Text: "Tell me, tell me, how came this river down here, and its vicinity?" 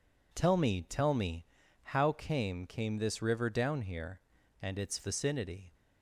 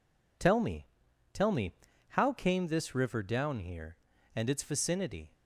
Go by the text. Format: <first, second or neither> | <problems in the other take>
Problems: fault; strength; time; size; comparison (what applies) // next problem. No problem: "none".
second | says "came" twice; at 2.6 s